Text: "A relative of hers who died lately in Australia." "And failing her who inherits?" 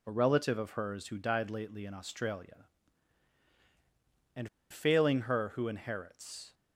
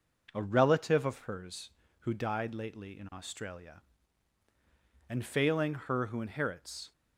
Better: second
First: pauses between "And" and "failing"; slight; at 4.4 s; 0.22 s long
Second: none

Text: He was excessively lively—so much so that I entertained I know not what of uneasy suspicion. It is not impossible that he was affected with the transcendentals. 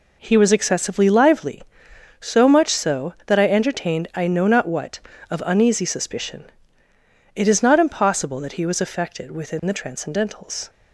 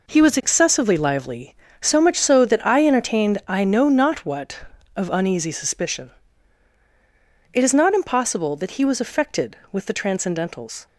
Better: second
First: says "within" for "with"; at 9.3 s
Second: none

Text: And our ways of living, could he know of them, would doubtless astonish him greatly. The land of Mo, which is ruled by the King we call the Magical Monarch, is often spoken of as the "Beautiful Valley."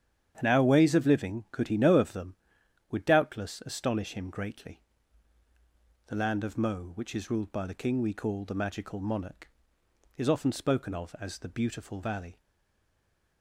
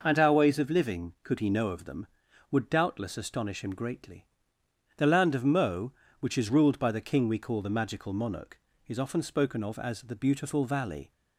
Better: second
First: starts louder than the rest; strong; until 1.3 s; 9 dB // stays silent after the last word; from 12.3 s on; 1.1 s long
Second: none

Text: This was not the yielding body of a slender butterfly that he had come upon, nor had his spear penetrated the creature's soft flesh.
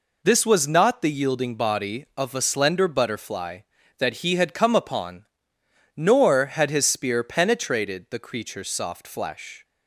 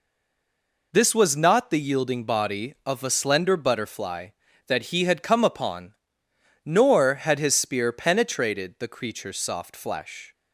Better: first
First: none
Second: stays silent before the first word; slight; until 0.9 s; 0.9 s long

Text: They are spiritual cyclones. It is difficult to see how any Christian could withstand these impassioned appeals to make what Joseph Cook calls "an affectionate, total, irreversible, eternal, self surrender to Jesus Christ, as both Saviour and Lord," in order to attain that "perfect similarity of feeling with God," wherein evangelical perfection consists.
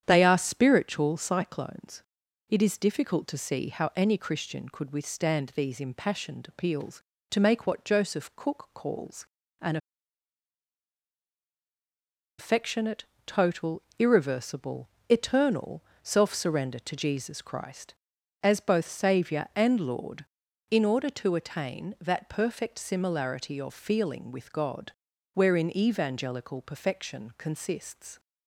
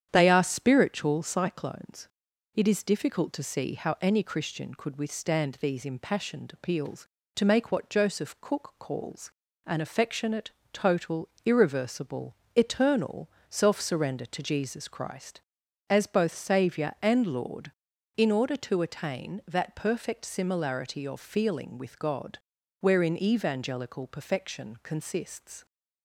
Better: second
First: starts louder than the rest; strong; until 1.0 s; 9 dB // pauses between "calls" and "an"; slight; at 9.2 s; 0.36 s long // pauses between "an" and "affectionate"; strong; at 9.7 s; 2.6 s long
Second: starts louder than the rest; strong; until 1.1 s; 9 dB // pauses between "calls" and "an"; slight; at 9.3 s; 0.36 s long

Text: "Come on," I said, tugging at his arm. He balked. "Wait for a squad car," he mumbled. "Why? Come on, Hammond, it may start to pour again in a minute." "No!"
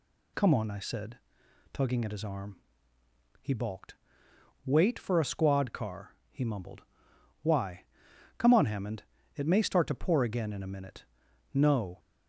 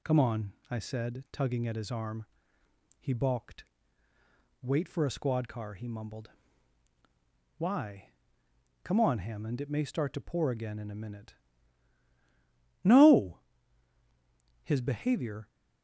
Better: first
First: none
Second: goes on to say "His behavior"; noticeable; from 14.6 s on; 0.84 s long

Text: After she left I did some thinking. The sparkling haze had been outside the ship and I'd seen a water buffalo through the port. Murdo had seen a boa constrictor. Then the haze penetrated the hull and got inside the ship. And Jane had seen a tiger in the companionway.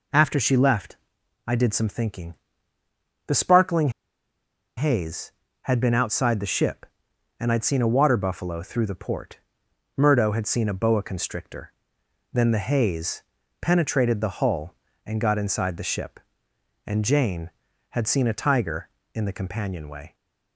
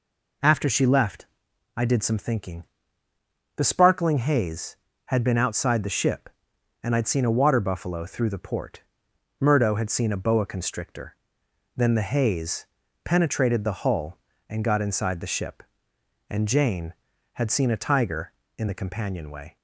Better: second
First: pauses between "left" and "I"; noticeable; at 0.9 s; 0.50 s long // pauses between "sparkling" and "haze"; noticeable; at 3.8 s; 0.87 s long // pauses between "haze" and "penetrated"; at 13.2 s; 0.38 s long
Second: pauses between "left" and "I"; noticeable; at 1.2 s; 0.50 s long // pauses between "haze" and "penetrated"; at 12.6 s; 0.38 s long

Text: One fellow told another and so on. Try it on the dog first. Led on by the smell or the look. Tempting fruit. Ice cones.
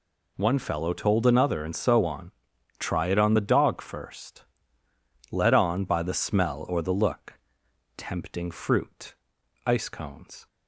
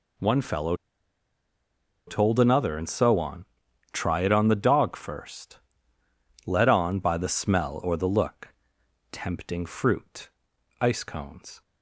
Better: first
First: none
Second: pauses between "fellow" and "told"; strong; at 0.7 s; 1.3 s long

